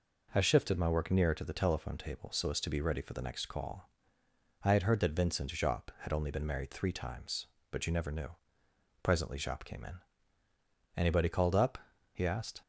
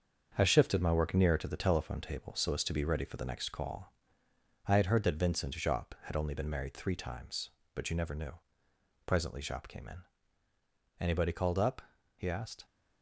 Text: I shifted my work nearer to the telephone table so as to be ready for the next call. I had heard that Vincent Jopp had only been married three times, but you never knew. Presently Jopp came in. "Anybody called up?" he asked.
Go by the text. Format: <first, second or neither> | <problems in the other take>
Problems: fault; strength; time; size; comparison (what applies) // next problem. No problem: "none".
first | gets quieter; throughout; 7 dB